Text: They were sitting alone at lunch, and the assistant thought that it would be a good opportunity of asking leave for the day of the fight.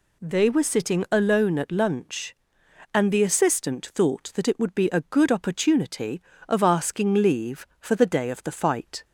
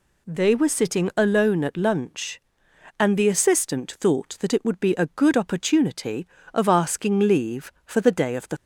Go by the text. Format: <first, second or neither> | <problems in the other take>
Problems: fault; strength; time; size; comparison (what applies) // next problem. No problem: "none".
first | stops before "fight"; at 8.5 s